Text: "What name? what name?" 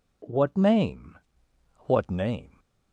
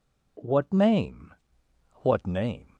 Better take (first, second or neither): neither